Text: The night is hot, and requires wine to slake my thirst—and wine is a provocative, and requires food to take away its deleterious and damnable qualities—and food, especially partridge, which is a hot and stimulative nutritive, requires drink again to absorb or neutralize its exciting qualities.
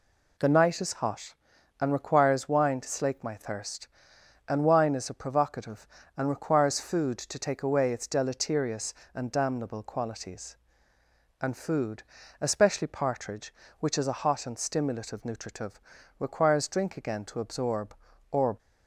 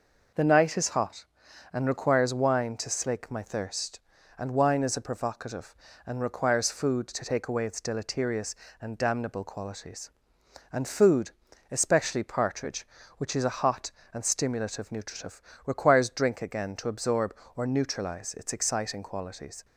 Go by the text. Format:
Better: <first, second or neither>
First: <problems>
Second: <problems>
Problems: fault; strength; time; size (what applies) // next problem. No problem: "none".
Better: second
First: stops before "neutralize its exciting qualities"; at 18.5 s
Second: none